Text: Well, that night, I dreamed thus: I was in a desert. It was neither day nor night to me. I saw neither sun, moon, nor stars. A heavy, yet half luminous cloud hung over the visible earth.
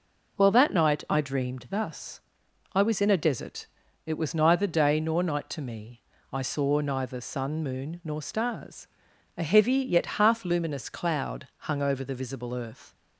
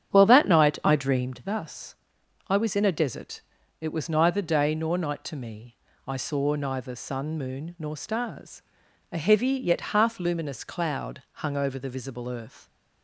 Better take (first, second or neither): first